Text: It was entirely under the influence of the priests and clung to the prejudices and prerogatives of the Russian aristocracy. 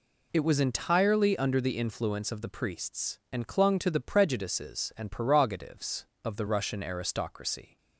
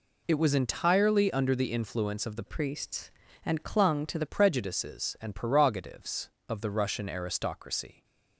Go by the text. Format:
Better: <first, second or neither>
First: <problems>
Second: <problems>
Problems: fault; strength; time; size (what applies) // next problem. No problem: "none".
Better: first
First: none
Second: changes voice from "priests" to "the"; from 2.4 to 4.2 s; 1.8 s long